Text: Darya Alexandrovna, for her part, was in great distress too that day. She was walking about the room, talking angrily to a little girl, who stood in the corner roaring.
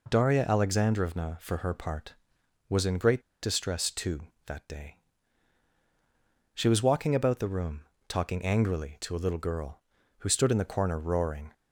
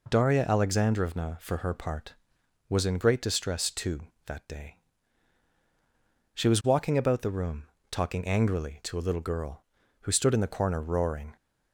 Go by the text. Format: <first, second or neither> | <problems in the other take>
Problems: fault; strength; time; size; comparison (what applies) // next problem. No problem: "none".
second | pauses between "great" and "distress"; slight; at 3.2 s; 0.21 s long